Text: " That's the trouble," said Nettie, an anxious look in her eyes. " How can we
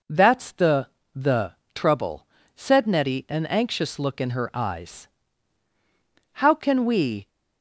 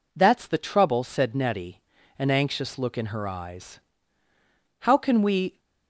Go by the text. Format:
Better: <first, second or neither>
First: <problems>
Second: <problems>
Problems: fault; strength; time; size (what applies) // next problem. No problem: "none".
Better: second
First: says "the" twice; at 1.1 s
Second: none